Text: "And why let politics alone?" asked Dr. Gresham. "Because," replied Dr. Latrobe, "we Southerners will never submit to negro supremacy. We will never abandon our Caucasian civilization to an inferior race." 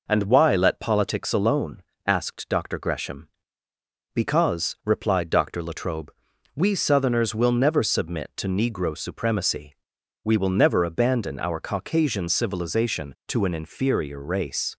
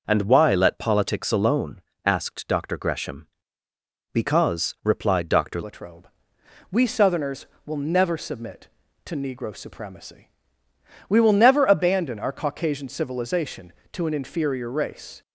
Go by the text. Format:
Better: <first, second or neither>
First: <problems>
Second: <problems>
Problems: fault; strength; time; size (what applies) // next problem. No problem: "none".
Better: first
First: none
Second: changes voice at "Latrobe"; from 5.6 s on; 9.6 s long